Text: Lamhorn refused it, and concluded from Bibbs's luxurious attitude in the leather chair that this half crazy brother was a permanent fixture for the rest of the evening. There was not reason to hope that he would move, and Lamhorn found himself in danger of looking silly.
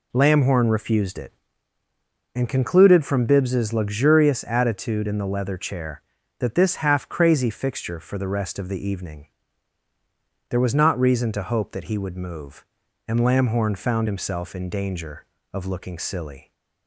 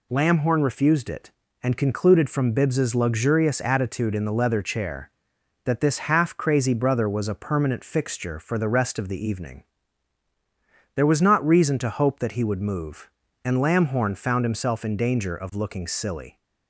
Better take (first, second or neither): second